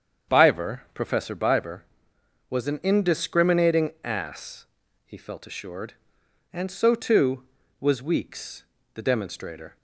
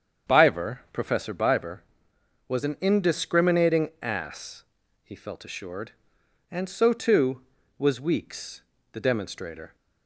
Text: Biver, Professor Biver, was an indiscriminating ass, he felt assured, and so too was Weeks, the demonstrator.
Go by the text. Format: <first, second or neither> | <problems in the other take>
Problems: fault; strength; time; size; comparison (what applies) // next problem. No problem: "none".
neither | starts louder than the rest; strong; the same in both